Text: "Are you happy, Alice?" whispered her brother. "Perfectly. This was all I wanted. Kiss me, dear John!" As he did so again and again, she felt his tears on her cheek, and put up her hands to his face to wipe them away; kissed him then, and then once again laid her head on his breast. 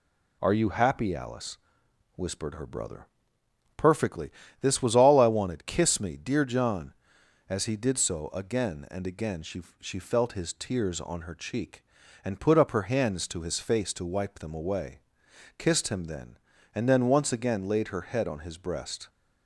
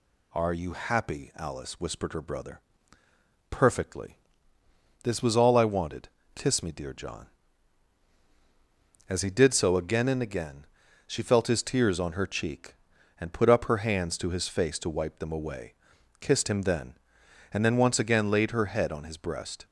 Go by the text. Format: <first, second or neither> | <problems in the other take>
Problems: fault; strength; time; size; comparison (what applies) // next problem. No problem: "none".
second | says "she" twice; at 9.8 s